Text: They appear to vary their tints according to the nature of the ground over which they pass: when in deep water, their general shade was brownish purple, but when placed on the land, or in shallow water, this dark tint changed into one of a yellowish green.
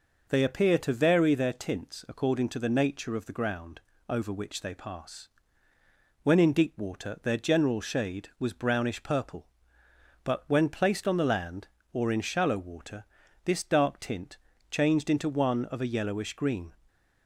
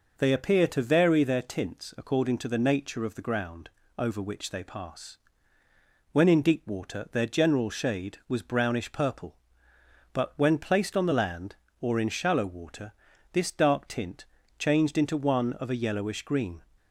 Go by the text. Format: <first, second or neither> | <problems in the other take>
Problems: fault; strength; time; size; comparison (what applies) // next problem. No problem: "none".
neither | pauses between "ground" and "over"; slight; the same in both // pauses between "tint" and "changed"; slight; the same in both